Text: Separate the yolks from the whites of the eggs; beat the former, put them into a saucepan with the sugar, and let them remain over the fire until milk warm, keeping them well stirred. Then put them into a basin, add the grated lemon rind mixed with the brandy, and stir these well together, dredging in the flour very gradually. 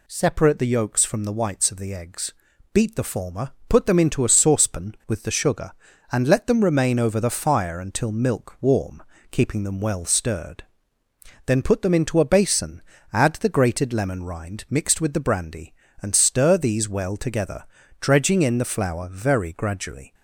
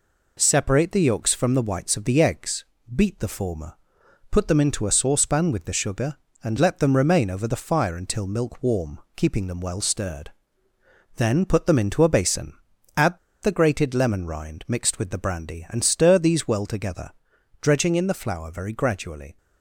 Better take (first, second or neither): first